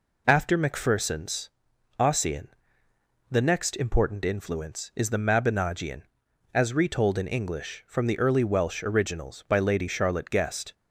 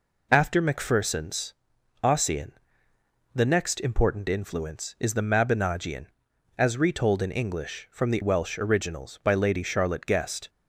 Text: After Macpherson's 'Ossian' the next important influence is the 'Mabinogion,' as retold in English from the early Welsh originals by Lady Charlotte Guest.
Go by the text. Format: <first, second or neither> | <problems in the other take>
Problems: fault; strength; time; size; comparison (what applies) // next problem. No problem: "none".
first | pauses between "Macpherson's" and "Ossian"; noticeable; at 1.5 s; 0.48 s long; noticeable in the first // pauses between "Ossian" and "the"; noticeable; at 2.4 s; 0.86 s long; noticeable in the first // skips "early"; at 8.2 s